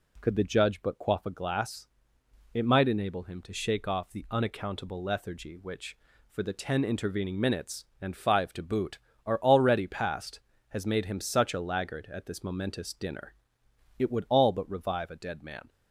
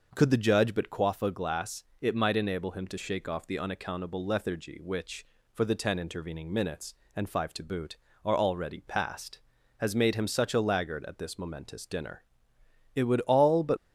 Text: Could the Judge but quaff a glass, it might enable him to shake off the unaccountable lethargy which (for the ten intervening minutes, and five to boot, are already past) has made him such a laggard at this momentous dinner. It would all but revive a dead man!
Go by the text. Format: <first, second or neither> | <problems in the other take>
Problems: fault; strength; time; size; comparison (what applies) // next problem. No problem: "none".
first | stops before "revive a dead man"; at 13.7 s